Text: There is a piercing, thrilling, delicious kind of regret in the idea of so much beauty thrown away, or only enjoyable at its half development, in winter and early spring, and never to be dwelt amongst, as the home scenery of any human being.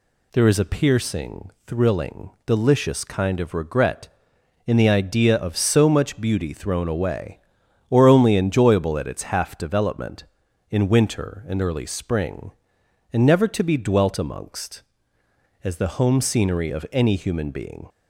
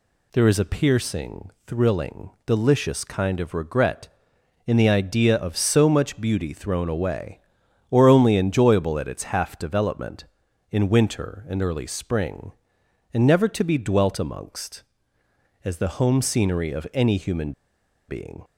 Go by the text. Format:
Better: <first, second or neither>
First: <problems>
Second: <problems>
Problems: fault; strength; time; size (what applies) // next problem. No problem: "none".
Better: first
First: none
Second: pauses between "human" and "being"; noticeable; at 17.5 s; 0.56 s long